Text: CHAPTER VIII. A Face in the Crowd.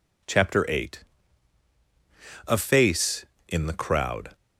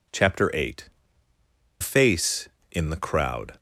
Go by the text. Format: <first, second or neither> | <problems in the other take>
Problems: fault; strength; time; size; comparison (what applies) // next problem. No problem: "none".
first | skips "A"; at 1.3 s